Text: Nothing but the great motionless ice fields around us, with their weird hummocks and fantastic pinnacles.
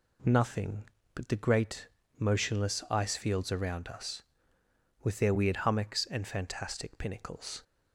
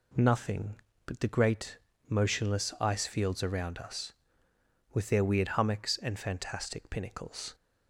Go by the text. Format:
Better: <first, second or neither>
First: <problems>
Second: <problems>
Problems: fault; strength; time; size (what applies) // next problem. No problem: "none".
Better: neither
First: pauses between "great" and "motionless"; slight; at 1.8 s; 0.32 s long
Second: pauses between "great" and "motionless"; slight; at 1.7 s; 0.32 s long